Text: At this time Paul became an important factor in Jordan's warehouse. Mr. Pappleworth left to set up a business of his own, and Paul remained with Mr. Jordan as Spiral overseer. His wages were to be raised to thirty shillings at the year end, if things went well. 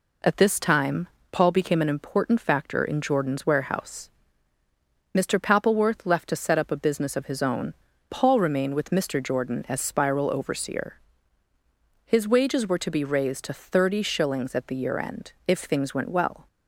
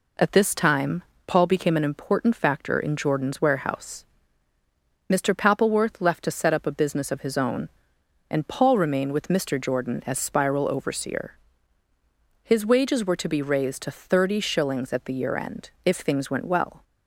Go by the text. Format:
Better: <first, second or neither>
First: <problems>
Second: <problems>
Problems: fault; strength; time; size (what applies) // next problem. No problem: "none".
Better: second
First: pauses between "time" and "Paul"; slight; at 1.0 s; 0.24 s long // skips "and"; at 7.9 s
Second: pauses between "time" and "Paul"; slight; at 1.0 s; 0.24 s long